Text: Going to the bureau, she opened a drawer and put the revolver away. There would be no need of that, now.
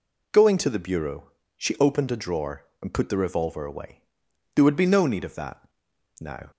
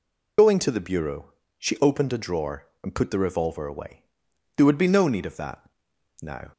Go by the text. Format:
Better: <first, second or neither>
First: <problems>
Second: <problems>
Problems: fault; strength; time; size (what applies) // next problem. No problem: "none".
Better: first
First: none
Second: loses the start of "Going"; at 0.3 s; 65 ms